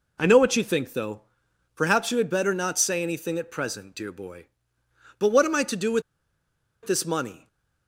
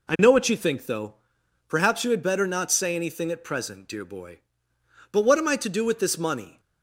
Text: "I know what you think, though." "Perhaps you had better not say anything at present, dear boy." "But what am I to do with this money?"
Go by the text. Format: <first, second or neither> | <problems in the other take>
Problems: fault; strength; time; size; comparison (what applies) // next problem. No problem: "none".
second | pauses between "with" and "this"; noticeable; at 6.0 s; 0.82 s long // stays silent after the last word; slight; from 7.3 s on; 0.5 s long